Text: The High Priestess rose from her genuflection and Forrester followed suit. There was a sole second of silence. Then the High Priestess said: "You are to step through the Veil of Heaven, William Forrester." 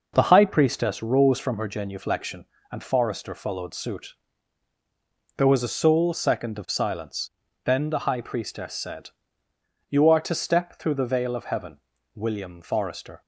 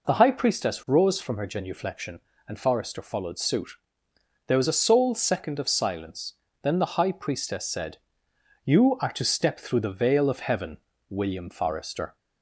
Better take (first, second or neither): neither